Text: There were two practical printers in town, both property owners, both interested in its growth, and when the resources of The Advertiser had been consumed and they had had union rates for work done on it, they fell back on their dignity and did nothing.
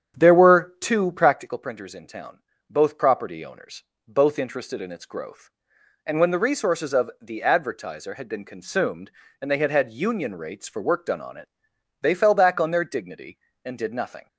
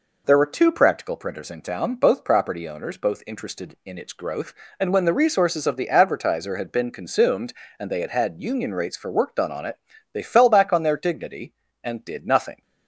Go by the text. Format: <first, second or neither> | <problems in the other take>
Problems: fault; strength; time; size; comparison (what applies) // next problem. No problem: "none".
second | starts louder than the rest; strong; until 1.6 s; 8.5 dB